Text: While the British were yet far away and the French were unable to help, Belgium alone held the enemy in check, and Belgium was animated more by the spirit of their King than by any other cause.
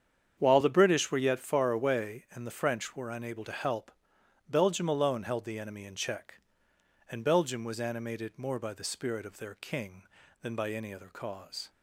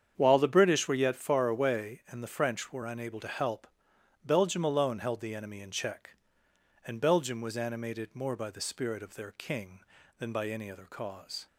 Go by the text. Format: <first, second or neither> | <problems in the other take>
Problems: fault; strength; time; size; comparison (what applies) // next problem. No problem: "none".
neither | starts louder than the rest; strong; the same in both